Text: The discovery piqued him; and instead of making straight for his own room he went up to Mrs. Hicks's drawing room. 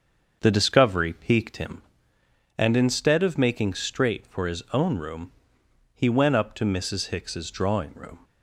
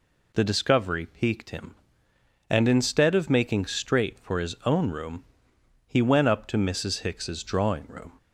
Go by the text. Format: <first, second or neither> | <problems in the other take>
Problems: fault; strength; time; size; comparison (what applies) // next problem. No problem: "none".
second | starts louder than the rest; until 1.9 s; 6.5 dB // pauses between "room" and "he"; noticeable; at 5.3 s; 0.62 s long; noticeable in the second